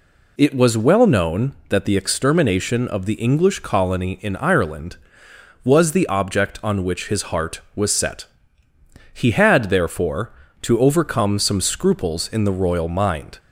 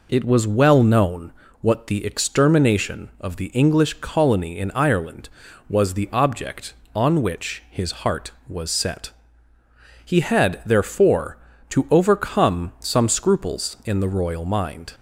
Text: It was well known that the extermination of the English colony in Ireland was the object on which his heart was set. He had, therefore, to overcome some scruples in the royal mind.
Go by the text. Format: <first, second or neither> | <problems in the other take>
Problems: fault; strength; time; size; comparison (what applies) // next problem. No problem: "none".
first | says "what" for "that"; at 1.6 s